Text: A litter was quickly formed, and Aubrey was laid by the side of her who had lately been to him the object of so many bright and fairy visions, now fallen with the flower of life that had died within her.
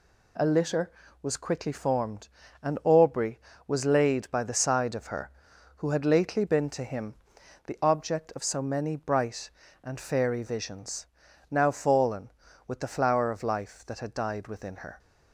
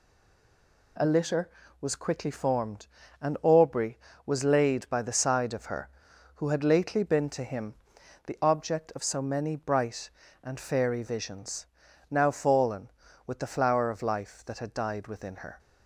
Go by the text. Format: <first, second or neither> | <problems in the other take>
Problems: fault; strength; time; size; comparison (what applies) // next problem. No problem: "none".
first | stays silent before the first word; slight; until 0.9 s; 0.9 s long // pauses between "him" and "the"; noticeable; at 7.7 s; 0.52 s long; noticeable in the first